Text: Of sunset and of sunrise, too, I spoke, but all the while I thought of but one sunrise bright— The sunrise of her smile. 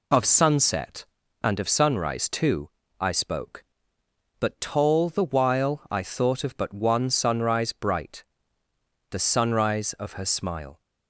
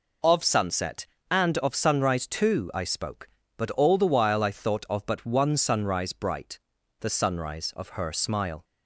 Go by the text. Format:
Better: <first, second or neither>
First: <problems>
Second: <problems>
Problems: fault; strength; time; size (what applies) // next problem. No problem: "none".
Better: second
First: says "tall" for "all"; at 4.6 s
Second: none